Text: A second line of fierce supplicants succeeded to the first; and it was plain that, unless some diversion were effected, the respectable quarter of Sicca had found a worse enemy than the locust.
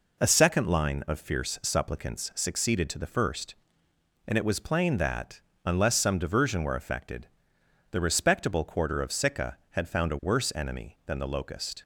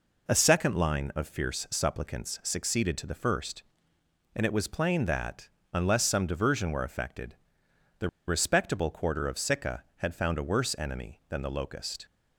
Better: first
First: none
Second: pauses between "the" and "respectable"; slight; at 8.0 s; 0.18 s long

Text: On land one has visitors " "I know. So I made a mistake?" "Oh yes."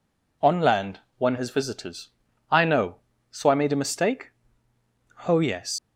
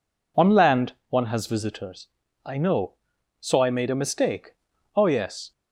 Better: second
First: pauses between "land" and "one"; slight; at 1.0 s; 0.16 s long // leaves "yes" unfinished; at 5.7 s; 105 ms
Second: pauses between "land" and "one"; slight; at 0.9 s; 0.16 s long

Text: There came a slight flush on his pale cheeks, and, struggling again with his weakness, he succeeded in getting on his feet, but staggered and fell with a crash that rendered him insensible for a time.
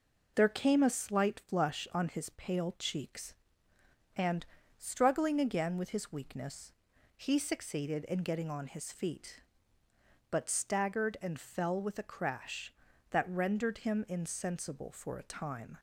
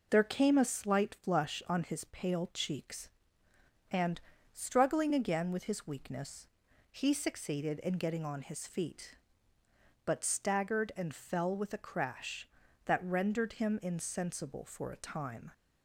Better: neither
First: none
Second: none

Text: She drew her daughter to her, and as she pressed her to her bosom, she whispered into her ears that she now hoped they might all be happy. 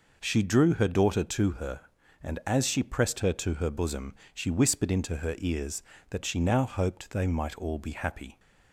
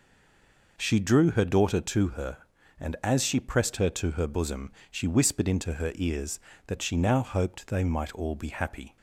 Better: first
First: none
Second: stays silent before the first word; slight; until 0.7 s; 0.7 s long

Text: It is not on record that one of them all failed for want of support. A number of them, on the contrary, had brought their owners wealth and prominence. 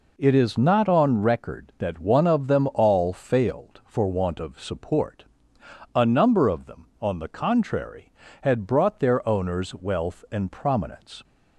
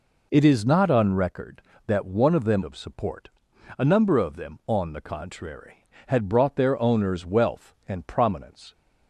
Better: first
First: none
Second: skips "all failed for want"; at 2.6 s

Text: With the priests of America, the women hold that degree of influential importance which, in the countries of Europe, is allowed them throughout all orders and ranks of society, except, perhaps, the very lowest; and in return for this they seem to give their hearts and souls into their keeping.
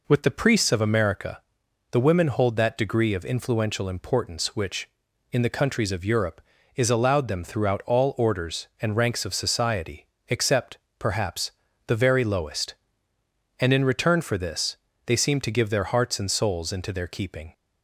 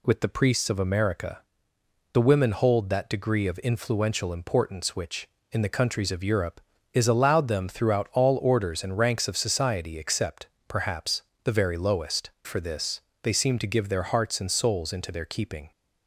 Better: first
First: pauses between "this" and "they"; slight; at 14.7 s; 0.30 s long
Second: skips "and in return"; at 12.3 s // pauses between "this" and "they"; slight; at 13.0 s; 0.22 s long

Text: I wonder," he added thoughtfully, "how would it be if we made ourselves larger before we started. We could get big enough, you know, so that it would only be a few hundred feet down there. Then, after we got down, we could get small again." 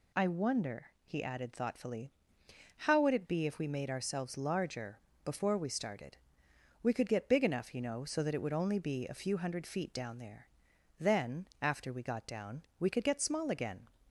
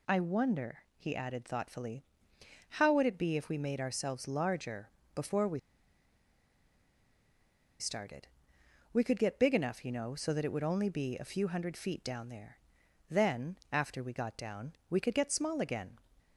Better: first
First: pauses between "larger" and "before"; slight; at 4.9 s; 0.26 s long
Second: pauses between "larger" and "before"; slight; at 4.8 s; 0.26 s long // pauses between "we" and "started"; strong; at 5.5 s; 2.2 s long

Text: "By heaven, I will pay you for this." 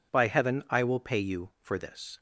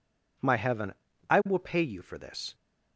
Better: first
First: none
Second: says "My" for "By"; at 0.3 s

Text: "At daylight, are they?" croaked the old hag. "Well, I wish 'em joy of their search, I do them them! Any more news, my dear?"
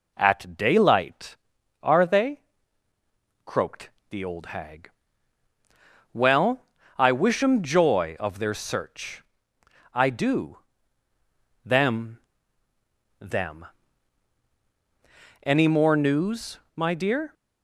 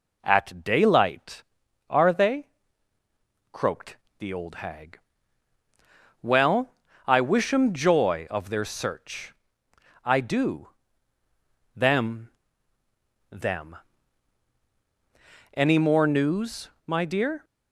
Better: neither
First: pauses between "croaked" and "the"; slight; at 3.8 s; 0.22 s long // pauses between "do" and "them"; at 10.5 s; 1.0 s long // pauses between "them" and "them"; at 12.1 s; 1.0 s long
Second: pauses between "croaked" and "the"; slight; at 3.9 s; 0.24 s long // pauses between "do" and "them"; at 10.6 s; 1.0 s long // pauses between "them" and "them"; at 12.2 s; 1.0 s long

